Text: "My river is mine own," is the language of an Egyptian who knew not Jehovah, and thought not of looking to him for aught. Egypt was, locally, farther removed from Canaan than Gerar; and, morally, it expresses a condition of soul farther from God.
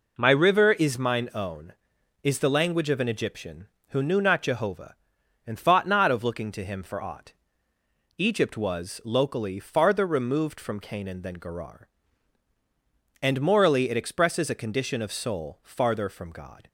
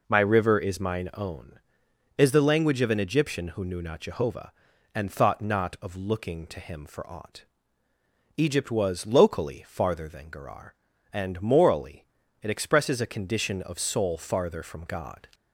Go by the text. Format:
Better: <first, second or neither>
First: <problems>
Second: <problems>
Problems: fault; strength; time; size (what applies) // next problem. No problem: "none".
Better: first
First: none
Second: skips "removed from Canaan"; at 10.0 s